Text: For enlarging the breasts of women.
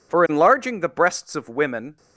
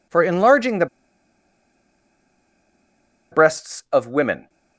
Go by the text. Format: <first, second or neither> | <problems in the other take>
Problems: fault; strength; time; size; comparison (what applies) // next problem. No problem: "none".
first | pauses between "the" and "breasts"; strong; at 0.8 s; 2.4 s long